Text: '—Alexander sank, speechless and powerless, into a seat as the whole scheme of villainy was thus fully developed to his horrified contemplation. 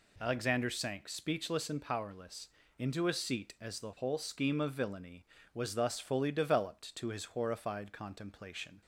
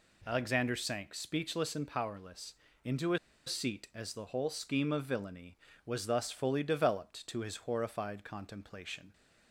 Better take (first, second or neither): first